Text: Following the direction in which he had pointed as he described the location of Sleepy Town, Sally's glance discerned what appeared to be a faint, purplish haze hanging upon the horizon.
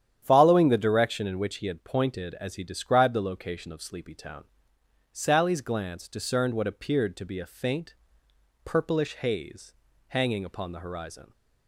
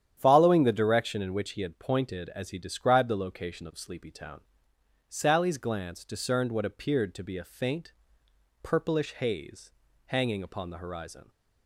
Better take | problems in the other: neither | starts louder than the rest; strong; the same in both // pauses between "haze" and "hanging"; the same in both

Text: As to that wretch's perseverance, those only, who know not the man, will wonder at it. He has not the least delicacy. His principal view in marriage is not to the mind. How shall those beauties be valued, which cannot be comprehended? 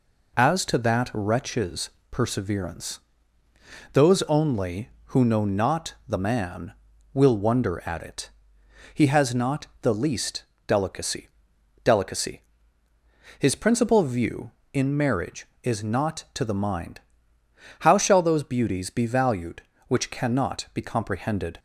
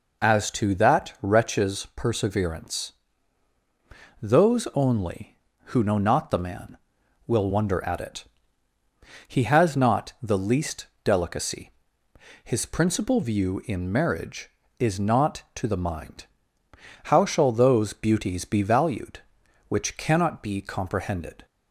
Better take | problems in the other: second | pauses between "wretch's" and "perseverance"; slight; at 1.9 s; 0.20 s long // pauses between "not" and "the"; slight; at 9.6 s; 0.16 s long // pauses between "least" and "delicacy"; slight; at 10.4 s; 0.22 s long; slight in the second // says "delicacy" twice; at 11.8 s

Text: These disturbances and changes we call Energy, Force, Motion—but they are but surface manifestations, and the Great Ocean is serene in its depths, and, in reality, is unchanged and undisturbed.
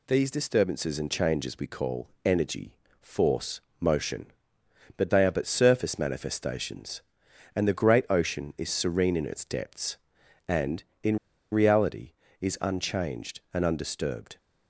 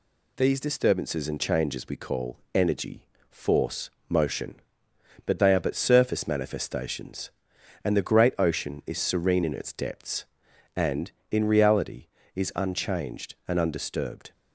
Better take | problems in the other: second | pauses between "call" and "Energy"; slight; at 2.0 s; 0.16 s long; slight in the second // pauses between "in" and "reality"; slight; at 11.1 s; 0.36 s long

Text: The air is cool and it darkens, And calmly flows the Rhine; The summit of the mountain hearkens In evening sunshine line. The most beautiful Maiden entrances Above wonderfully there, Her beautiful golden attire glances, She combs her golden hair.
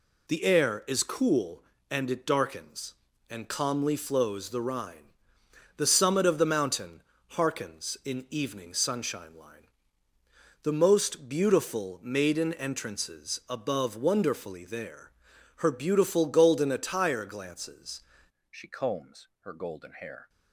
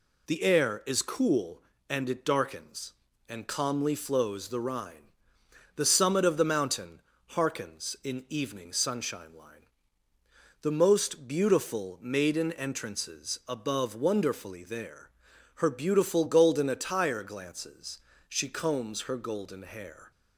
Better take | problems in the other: second | pauses between "mountain" and "hearkens"; slight; at 7.0 s; 0.28 s long; slight in the second // changes voice at "She"; from 18.5 s on; 1.7 s long // pauses between "combs" and "her"; slight; at 19.2 s; 0.16 s long

